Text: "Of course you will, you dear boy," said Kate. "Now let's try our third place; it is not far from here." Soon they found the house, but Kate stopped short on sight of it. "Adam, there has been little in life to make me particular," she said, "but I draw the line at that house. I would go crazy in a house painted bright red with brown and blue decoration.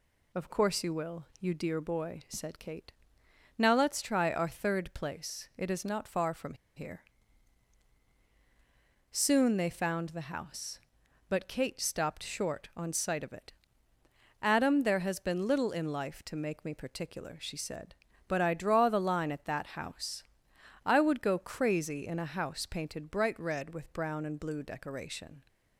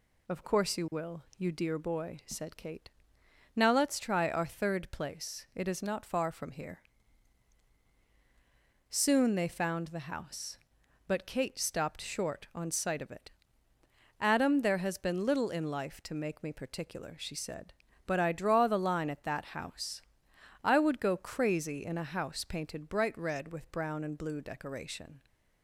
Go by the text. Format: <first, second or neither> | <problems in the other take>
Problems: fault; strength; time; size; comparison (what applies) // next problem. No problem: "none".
second | pauses between "from" and "here"; slight; at 6.5 s; 0.22 s long